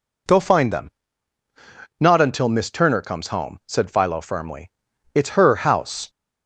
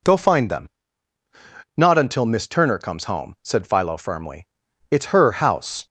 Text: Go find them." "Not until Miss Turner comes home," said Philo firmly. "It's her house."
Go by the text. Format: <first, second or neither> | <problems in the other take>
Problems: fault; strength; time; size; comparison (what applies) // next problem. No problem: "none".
neither | none